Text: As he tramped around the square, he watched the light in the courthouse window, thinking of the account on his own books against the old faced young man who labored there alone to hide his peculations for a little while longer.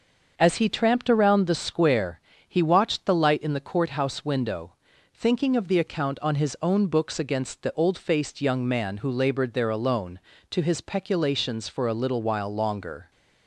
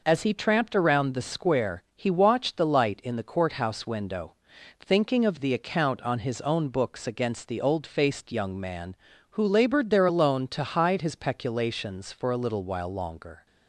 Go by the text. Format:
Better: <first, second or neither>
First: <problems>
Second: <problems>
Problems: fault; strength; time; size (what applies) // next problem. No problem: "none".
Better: second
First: starts louder than the rest; until 1.3 s; 6.5 dB // skips "hide"; at 10.6 s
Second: none